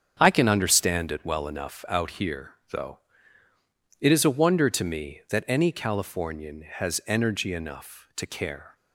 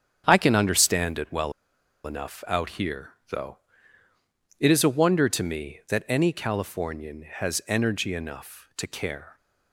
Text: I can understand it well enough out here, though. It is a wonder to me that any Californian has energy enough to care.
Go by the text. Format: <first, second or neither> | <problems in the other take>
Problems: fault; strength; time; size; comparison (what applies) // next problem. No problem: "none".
first | starts louder than the rest; strong; until 1.2 s; 8 dB; strong in the first // pauses between "well" and "enough"; noticeable; at 1.5 s; 0.52 s long